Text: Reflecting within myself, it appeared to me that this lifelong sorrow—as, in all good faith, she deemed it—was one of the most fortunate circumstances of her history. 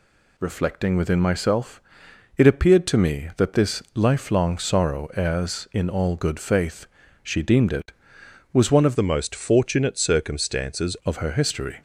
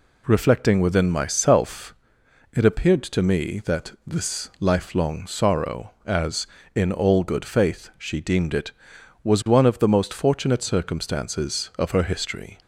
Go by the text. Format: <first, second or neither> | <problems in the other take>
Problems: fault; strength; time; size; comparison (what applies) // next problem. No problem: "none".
second | changes voice from "the" to "circumstances"; from 8.9 to 10.9 s; 2.0 s long